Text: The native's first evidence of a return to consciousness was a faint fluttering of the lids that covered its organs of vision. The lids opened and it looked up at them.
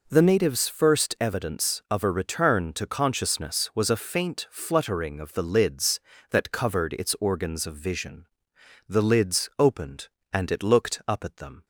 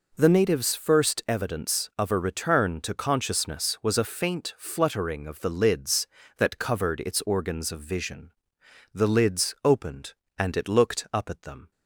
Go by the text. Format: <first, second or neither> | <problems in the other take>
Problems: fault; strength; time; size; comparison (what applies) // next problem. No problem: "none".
neither | none